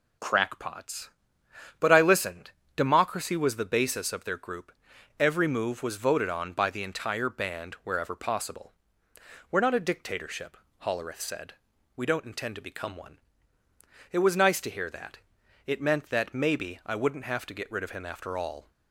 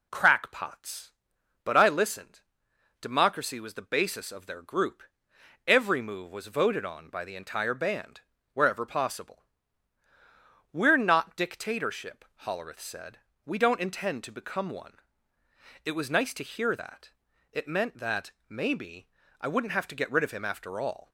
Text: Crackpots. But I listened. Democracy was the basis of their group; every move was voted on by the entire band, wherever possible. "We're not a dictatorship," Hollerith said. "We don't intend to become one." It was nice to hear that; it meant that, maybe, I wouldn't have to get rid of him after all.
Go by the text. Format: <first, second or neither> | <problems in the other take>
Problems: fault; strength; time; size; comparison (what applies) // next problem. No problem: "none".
first | skips "a"; at 11.3 s